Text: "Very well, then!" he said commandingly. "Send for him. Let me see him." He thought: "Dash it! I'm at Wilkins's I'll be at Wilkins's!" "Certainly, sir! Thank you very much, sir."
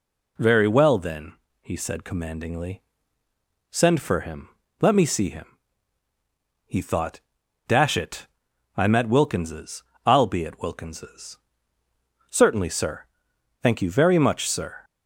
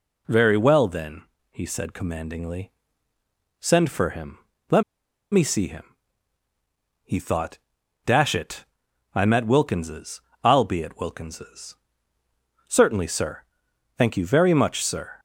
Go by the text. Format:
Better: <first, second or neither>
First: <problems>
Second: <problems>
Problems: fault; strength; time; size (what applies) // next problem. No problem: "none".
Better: first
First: pauses between "Wilkins's" and "I'll"; slight; at 9.8 s; 0.24 s long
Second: pauses between "Let" and "me"; noticeable; at 4.8 s; 0.50 s long // pauses between "Wilkins's" and "I'll"; slight; at 10.1 s; 0.24 s long